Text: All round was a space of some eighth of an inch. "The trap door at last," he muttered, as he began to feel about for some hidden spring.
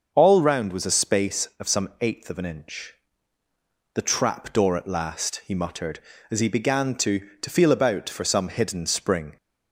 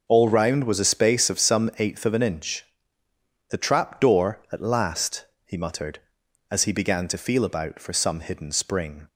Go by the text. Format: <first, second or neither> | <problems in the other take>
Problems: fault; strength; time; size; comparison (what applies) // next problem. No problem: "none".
second | starts louder than the rest; until 1.1 s; 6.5 dB // says "to" twice; at 7.4 s